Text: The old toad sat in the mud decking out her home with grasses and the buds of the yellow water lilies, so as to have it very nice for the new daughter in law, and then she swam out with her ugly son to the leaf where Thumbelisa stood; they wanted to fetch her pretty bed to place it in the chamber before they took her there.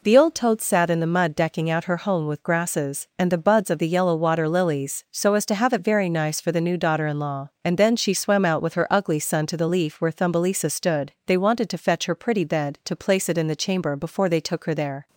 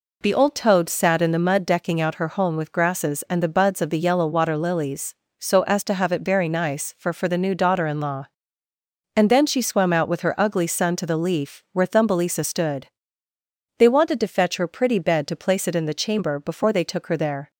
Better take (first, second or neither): first